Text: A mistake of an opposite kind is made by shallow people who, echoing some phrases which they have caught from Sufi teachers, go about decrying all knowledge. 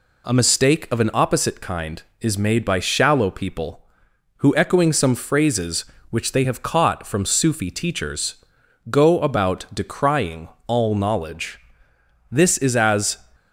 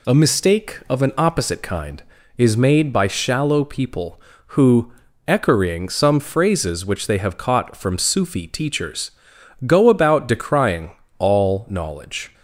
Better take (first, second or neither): second